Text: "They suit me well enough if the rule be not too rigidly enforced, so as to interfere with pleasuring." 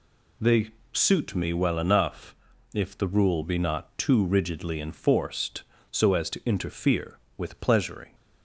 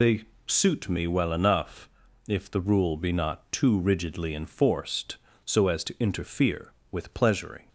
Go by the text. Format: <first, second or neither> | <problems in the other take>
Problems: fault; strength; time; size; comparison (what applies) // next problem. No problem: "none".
first | loses the start of "They"; at 0.0 s; 60 ms // pauses between "They" and "suit"; slight; at 0.2 s; 0.20 s long; slight in the first // pauses between "enough" and "if"; at 1.8 s; 0.38 s long; also in the first